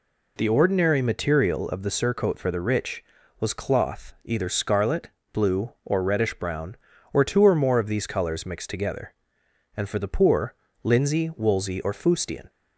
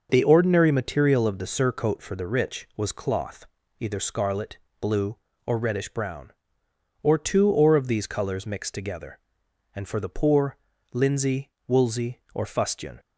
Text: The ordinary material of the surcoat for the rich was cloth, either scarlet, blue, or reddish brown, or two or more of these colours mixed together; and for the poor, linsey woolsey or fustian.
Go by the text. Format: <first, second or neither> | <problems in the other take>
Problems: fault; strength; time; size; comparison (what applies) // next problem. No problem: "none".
first | starts louder than the rest; noticeable; until 1.1 s; 6 dB // skips "more"; at 7.7 s // pauses between "linsey" and "woolsey"; slight; at 11.5 s; 0.18 s long